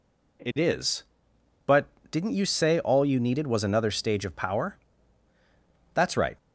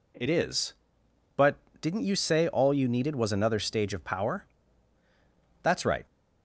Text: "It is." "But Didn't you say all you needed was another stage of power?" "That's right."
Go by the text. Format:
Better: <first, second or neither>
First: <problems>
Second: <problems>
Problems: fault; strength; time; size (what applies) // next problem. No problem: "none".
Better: neither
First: pauses between "But" and "Didn't"; slight; at 1.8 s; 0.24 s long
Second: pauses between "But" and "Didn't"; slight; at 1.5 s; 0.24 s long